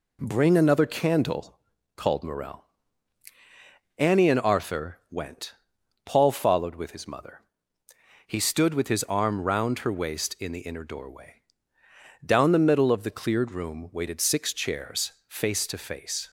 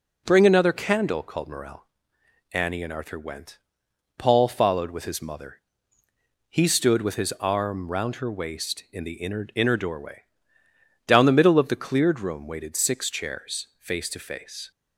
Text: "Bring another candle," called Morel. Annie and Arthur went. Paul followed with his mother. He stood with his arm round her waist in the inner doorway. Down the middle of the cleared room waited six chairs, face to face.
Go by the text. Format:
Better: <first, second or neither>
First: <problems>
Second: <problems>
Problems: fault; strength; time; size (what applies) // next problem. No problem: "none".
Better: first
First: none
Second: says "inner" twice; at 9.5 s